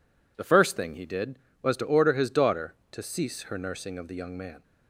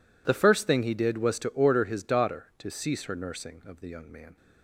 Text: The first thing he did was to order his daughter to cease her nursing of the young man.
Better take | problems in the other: neither | none

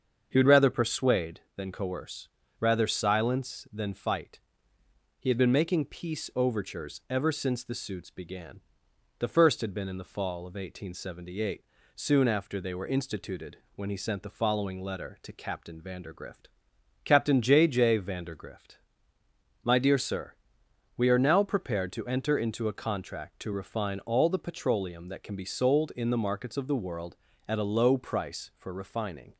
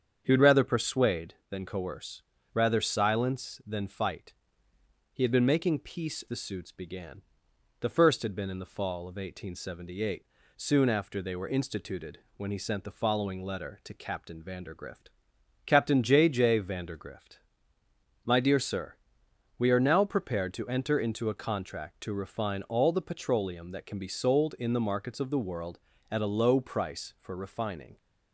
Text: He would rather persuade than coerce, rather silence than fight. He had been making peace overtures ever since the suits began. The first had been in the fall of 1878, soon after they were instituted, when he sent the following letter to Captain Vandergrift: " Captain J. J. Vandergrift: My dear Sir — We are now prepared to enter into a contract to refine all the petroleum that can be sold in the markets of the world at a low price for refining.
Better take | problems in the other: first | starts louder than the rest; strong; until 1.2 s; 7.5 dB; also in the first // skips "overtures ever since"; at 6.2 s

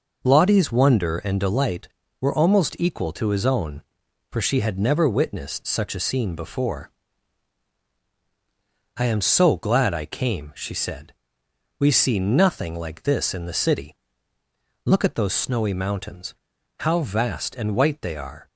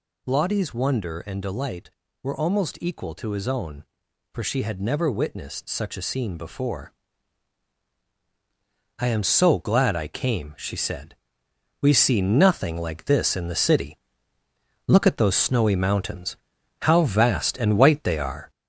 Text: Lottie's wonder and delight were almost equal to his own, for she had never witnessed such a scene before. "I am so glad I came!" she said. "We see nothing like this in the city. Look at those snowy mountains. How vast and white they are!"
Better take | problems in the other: first | gets louder; noticeable; throughout; 4.5 dB

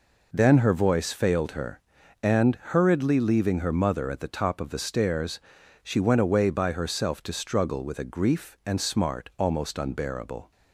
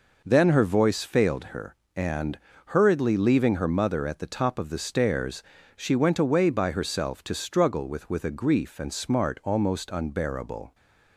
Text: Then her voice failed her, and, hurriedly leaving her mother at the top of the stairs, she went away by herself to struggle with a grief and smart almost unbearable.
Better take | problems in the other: first | says "with" twice; at 8.0 s

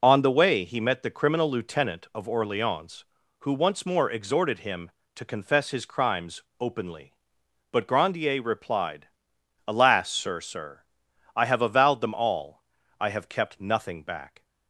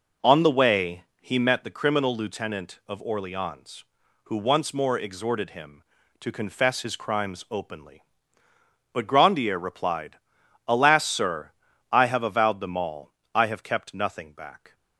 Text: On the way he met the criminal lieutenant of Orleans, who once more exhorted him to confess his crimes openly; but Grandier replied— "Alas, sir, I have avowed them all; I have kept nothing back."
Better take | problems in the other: second | pauses between "crimes" and "openly"; slight; at 6.4 s; 0.18 s long // says "sir" twice; at 10.3 s

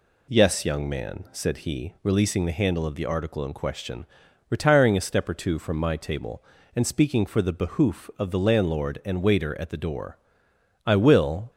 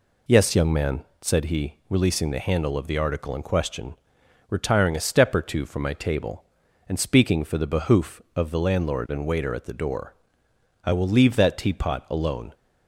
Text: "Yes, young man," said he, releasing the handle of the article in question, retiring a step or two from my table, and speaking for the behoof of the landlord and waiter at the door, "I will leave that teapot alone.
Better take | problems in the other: second | stops before "leave that teapot alone"; at 11.4 s

